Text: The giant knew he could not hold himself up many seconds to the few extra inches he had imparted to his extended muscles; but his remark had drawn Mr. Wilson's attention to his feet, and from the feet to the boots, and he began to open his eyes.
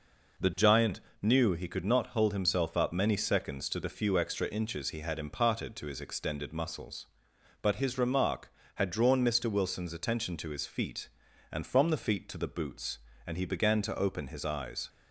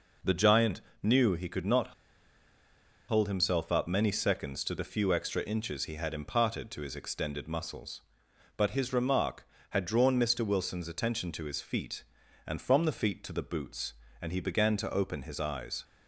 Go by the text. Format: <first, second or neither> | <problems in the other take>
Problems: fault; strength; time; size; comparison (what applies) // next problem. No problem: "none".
first | pauses between "giant" and "knew"; slight; at 0.8 s; 0.20 s long; slight in the first // pauses between "not" and "hold"; at 1.9 s; 1.1 s long